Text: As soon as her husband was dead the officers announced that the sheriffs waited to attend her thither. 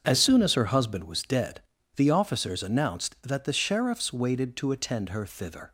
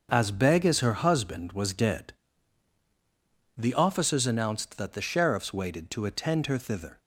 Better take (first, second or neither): first